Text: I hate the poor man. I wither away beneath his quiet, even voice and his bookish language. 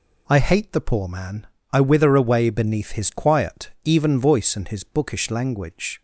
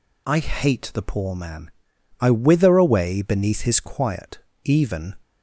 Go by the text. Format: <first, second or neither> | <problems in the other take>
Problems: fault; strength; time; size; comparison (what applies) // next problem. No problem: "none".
first | stops before "voice and his bookish language"; at 5.2 s